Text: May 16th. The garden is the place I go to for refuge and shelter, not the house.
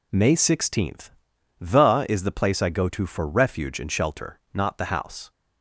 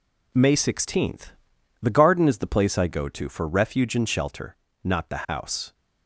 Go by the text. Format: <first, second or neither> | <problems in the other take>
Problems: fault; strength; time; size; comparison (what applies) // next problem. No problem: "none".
second | skips "garden"; at 2.0 s